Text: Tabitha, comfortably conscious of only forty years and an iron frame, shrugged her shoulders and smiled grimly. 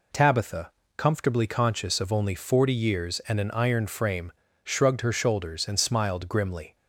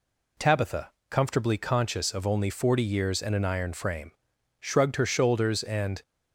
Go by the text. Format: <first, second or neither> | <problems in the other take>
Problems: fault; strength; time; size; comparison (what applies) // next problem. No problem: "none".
first | stops before "smiled grimly"; at 6.0 s